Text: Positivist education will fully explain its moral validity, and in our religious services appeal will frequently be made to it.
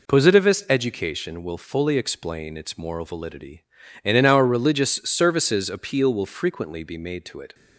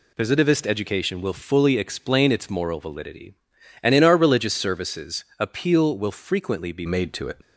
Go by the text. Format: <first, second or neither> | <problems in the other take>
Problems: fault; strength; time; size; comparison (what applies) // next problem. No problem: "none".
first | changes voice at "made"; from 6.8 s on; 0.5 s long